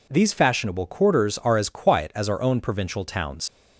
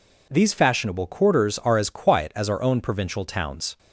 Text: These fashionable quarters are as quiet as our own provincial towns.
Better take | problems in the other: second | leaves "towns" unfinished; at 3.4 s; 100 ms

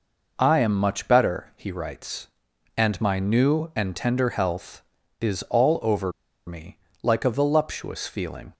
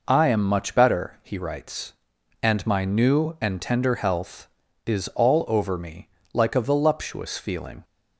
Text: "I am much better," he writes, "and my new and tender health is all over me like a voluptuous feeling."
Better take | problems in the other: second | pauses between "over" and "me"; slight; at 6.1 s; 0.35 s long // pauses between "me" and "like"; slight; at 6.7 s; 0.26 s long; slight in the second

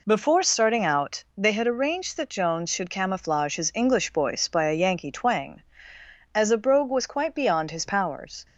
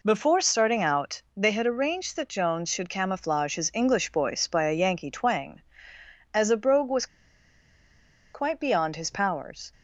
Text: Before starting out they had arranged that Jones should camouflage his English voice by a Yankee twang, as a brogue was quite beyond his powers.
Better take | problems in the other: first | pauses between "was" and "quite"; strong; at 7.0 s; 1.2 s long

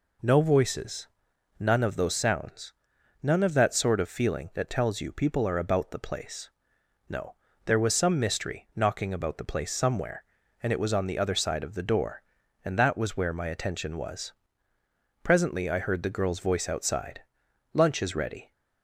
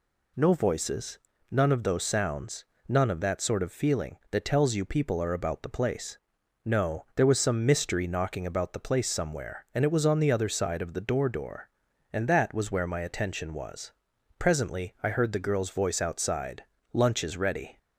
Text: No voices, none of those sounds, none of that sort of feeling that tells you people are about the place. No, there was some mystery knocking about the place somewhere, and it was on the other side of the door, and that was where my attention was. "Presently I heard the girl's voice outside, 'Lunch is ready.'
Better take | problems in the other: first | says "door" twice; at 11.2 s

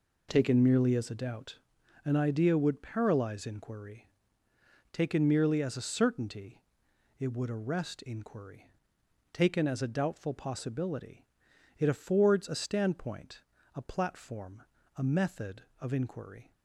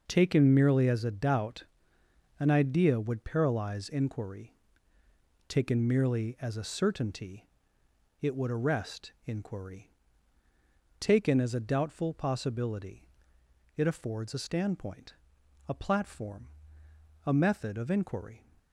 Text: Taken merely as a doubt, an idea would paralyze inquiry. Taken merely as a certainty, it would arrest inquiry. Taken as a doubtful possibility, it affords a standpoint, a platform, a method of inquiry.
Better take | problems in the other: neither | none

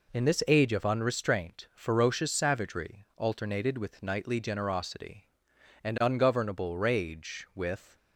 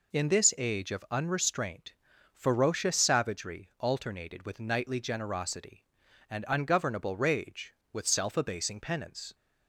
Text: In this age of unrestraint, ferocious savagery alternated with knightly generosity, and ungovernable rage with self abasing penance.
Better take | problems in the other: second | stops before "self abasing penance"; at 7.9 s

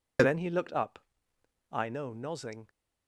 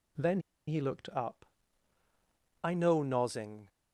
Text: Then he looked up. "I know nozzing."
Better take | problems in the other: first | pauses between "Then" and "he"; slight; at 0.4 s; 0.27 s long

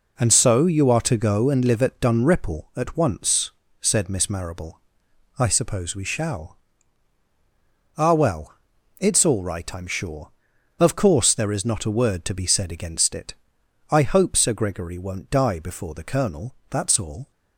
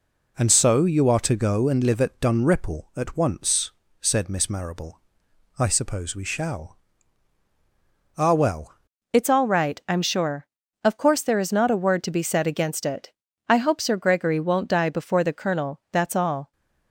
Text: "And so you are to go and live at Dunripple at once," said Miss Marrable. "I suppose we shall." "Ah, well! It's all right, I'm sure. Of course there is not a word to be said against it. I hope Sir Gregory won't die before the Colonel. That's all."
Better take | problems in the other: first | changes voice at "It's"; from 9.1 s on; 7.4 s long

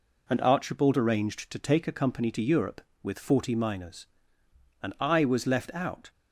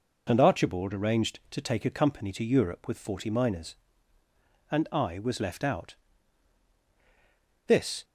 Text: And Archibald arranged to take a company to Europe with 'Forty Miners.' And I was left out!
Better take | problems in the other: first | goes on to say "This"; slight; from 7.6 s on; 0.38 s long

